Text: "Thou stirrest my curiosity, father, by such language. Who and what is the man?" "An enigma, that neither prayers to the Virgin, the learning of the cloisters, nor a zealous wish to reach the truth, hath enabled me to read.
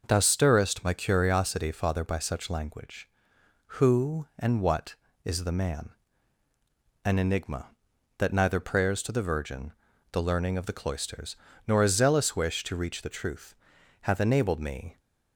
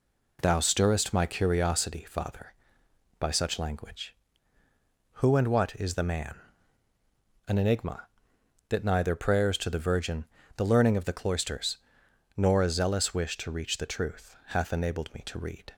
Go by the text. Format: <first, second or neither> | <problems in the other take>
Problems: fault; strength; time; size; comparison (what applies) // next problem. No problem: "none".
second | stops before "to read"; at 14.9 s